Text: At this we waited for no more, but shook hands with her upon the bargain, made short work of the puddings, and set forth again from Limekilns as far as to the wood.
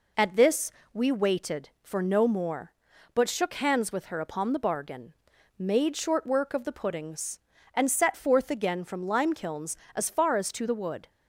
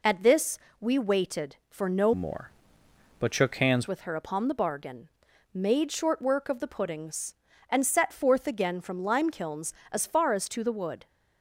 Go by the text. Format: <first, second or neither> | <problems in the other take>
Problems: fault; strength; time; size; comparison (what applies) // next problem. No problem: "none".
first | pauses between "this" and "we"; slight; at 0.5 s; 0.22 s long; slight in the first // changes voice from "more" to "hands"; from 2.1 to 3.8 s; 1.7 s long